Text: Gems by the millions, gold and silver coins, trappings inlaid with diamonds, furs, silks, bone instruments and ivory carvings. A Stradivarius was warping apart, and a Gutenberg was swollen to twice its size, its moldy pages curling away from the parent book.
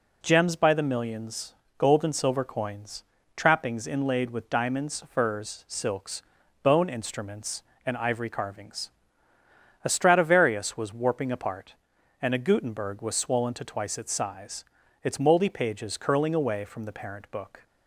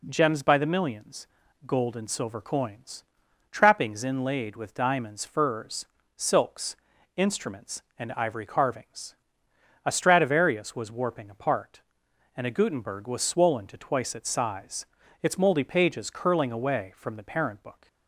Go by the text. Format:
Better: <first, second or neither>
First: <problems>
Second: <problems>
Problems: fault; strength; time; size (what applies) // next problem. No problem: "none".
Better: first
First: none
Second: skips "bone"; at 6.9 s